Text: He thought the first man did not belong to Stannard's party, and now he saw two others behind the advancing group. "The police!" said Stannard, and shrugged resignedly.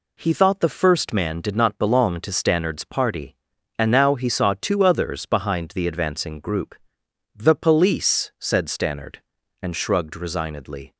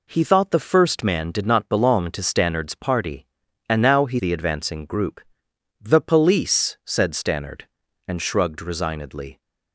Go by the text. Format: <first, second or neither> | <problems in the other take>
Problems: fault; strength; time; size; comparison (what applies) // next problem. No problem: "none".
first | skips "saw two others behind"; at 4.1 s